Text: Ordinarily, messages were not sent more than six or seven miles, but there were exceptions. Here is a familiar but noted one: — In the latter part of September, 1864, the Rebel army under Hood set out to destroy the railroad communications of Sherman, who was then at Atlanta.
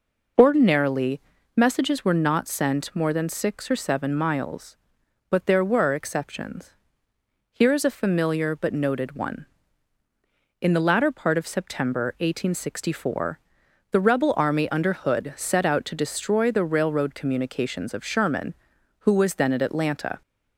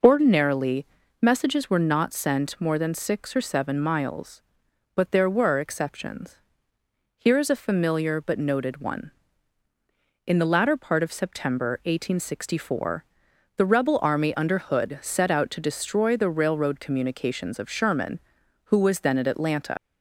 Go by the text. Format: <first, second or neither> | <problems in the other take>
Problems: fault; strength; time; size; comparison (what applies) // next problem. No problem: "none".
first | leaves "Atlanta" unfinished; at 19.7 s; 95 ms